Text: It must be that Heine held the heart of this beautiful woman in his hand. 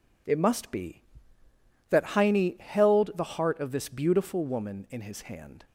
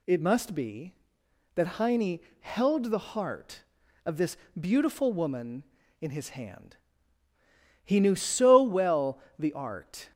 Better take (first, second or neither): first